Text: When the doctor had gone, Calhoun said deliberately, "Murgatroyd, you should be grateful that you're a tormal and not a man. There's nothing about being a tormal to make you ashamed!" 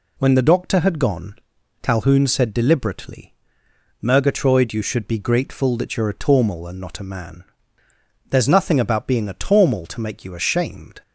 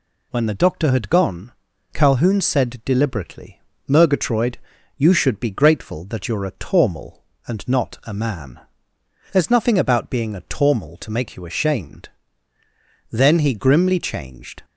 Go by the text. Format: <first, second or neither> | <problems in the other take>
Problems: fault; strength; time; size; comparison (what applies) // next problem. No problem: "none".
first | goes on to say "Then he grimly changed"; from 13.1 s on; 1.5 s long